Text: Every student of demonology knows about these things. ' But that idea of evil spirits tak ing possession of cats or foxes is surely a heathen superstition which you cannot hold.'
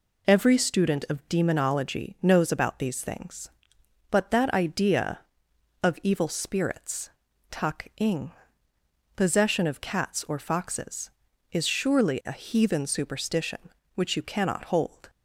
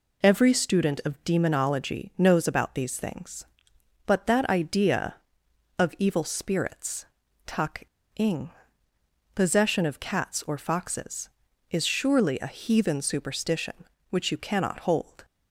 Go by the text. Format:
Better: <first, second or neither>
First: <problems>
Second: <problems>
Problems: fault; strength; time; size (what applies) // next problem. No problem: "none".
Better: first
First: pauses between "spirits" and "tak"; at 7.0 s; 0.40 s long // pauses between "ing" and "possession"; noticeable; at 8.2 s; 0.86 s long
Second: pauses between "spirits" and "tak"; at 7.0 s; 0.40 s long // pauses between "tak" and "ing"; slight; at 7.8 s; 0.29 s long // pauses between "ing" and "possession"; noticeable; at 8.4 s; 0.86 s long